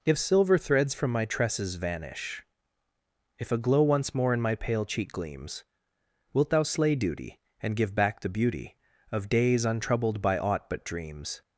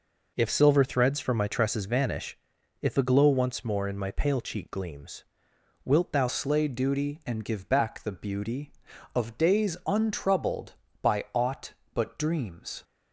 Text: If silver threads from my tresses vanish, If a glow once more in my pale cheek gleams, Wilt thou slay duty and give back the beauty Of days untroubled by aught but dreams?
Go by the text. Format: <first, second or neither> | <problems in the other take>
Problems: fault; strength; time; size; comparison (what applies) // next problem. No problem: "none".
first | changes voice at "slay"; from 6.2 s on; 6.6 s long